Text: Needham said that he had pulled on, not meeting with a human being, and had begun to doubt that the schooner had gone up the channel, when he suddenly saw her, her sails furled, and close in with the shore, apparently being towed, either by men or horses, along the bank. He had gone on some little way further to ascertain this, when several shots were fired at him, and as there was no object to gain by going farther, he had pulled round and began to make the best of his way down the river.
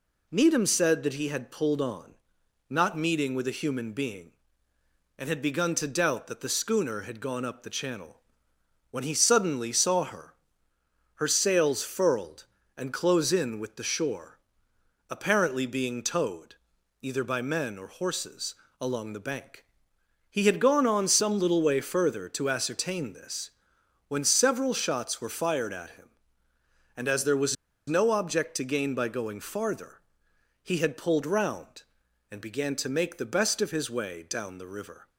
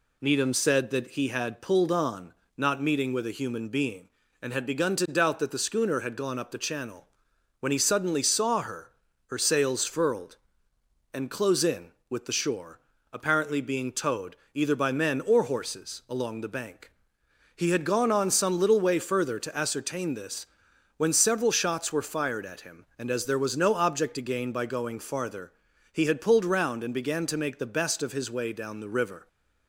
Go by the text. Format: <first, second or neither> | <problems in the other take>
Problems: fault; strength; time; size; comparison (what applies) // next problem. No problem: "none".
second | pauses between "was" and "no"; slight; at 27.5 s; 0.32 s long